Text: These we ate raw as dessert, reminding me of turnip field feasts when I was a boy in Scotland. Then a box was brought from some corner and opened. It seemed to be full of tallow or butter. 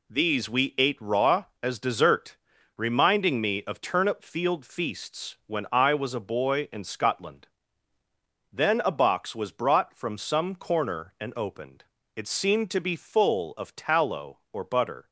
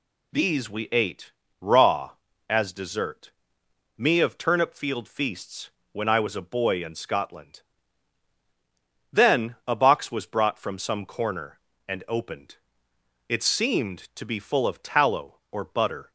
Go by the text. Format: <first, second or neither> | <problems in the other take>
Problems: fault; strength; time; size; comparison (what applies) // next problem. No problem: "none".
first | pauses between "ate" and "raw"; slight; at 1.3 s; 0.28 s long // skips "reminding"; at 3.6 s // pauses between "feasts" and "when"; slight; at 5.7 s; 0.22 s long